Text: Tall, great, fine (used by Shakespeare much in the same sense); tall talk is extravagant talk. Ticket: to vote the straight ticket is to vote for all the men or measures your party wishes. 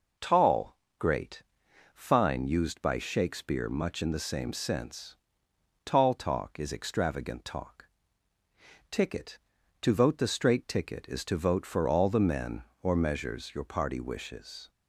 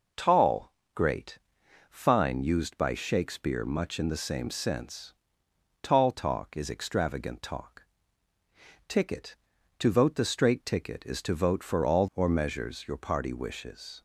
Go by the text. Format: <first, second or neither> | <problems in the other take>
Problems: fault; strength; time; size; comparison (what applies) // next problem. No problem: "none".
first | skips "the men"; at 12.0 s